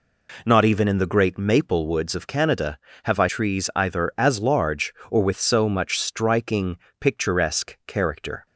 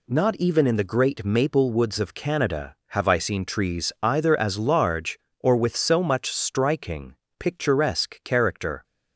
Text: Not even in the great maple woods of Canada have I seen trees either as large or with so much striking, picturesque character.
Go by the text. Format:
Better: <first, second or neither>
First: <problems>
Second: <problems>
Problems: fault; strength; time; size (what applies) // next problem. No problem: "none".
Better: second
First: skips "seen"; at 3.2 s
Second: none